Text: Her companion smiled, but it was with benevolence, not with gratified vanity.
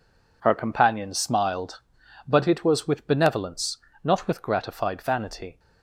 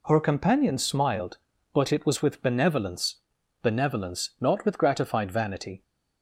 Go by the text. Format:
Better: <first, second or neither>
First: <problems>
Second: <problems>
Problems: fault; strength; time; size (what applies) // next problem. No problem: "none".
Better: first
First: none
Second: says "benevolence" twice; at 3.6 s